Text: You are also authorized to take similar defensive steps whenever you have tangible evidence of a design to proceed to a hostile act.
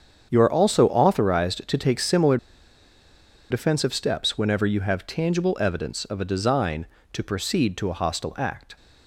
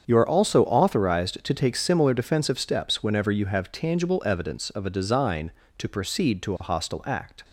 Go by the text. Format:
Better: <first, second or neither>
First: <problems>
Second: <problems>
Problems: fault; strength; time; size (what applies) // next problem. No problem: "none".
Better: second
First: starts louder than the rest; strong; until 1.3 s; 7.5 dB // pauses between "similar" and "defensive"; at 2.3 s; 1.1 s long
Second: starts louder than the rest; strong; until 1.0 s; 7.5 dB